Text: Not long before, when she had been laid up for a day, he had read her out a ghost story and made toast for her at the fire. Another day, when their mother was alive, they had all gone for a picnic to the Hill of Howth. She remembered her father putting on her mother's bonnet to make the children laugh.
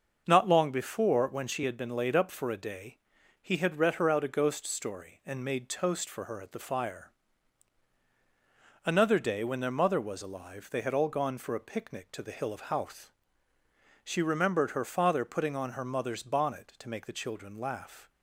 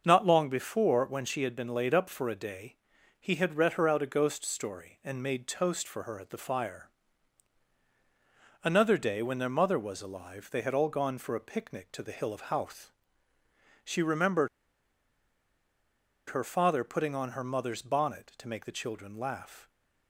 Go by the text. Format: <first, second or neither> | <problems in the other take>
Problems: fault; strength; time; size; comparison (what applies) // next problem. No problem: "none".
first | starts louder than the rest; until 1.0 s; 6.5 dB; also in the first // pauses between "remembered" and "her"; strong; at 14.4 s; 1.8 s long